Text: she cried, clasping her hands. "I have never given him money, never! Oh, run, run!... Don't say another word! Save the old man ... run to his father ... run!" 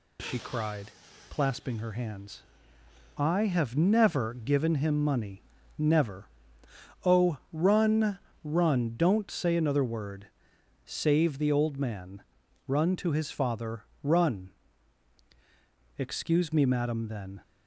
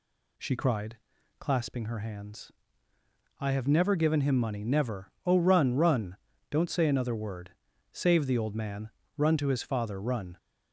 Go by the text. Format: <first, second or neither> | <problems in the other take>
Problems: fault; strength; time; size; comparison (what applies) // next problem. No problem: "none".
second | goes on to say "Excuse me madam then"; from 15.9 s on; 1.4 s long